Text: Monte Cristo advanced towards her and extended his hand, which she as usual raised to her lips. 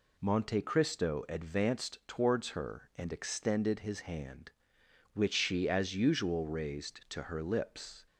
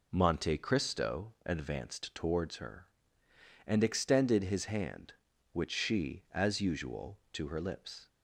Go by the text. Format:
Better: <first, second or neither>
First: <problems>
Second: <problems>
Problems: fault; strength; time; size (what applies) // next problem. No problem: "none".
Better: first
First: none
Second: skips "raised"; at 7.2 s